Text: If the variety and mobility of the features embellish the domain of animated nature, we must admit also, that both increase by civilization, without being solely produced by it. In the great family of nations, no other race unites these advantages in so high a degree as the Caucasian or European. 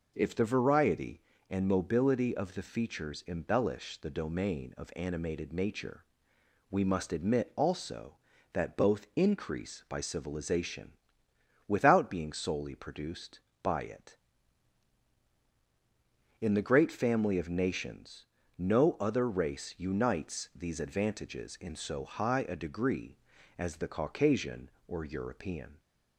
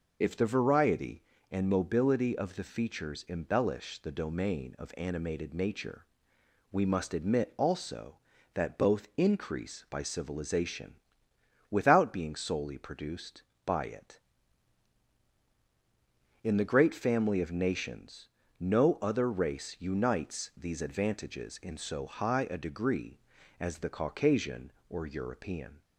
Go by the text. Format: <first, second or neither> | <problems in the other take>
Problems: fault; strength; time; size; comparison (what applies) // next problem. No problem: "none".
first | loses the start of "If"; at 0.2 s; 45 ms